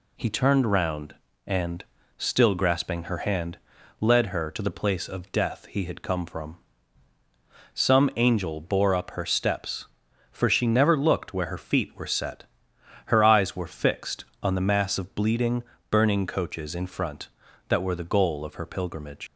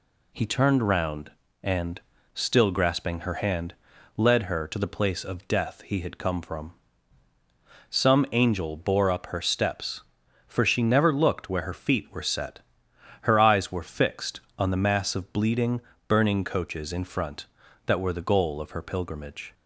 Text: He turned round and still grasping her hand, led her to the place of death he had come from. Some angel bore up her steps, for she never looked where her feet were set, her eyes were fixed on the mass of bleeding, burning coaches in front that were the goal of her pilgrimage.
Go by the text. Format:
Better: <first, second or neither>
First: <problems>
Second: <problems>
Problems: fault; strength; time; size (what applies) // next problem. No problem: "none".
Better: second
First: pauses between "and" and "still"; slight; at 1.8 s; 0.32 s long // leaves "pilgrimage" unfinished; at 19.2 s; 100 ms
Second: pauses between "and" and "still"; slight; at 2.0 s; 0.32 s long